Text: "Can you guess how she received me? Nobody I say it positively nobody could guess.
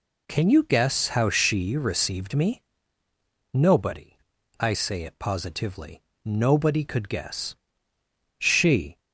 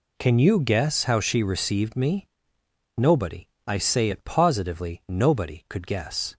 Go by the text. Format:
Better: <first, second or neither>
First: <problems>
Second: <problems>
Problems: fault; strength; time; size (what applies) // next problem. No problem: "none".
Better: second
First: pauses between "Nobody" and "I"; at 4.1 s; 0.42 s long // pauses between "positively" and "nobody"; slight; at 6.0 s; 0.36 s long // goes on to say "She"; noticeable; from 8.3 s on; 0.62 s long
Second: pauses between "Nobody" and "I"; slight; at 3.4 s; 0.20 s long